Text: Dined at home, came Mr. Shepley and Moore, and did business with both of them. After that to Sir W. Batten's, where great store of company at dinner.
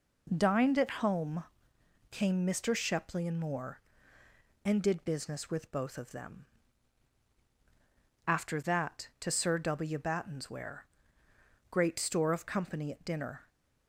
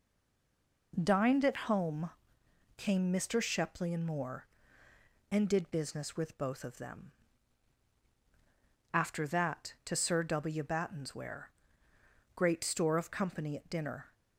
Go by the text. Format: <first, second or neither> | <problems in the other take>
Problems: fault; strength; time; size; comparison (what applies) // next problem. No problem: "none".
first | stays silent before the first word; slight; until 0.9 s; 0.9 s long // pauses between "where" and "great"; noticeable; at 11.4 s; 0.86 s long; noticeable in the first